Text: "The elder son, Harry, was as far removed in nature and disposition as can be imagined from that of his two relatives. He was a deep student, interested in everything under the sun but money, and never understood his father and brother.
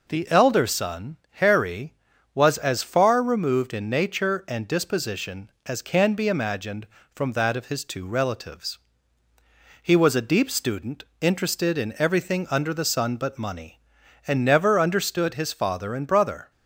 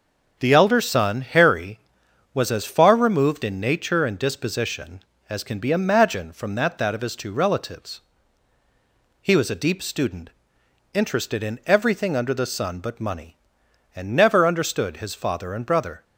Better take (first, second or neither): first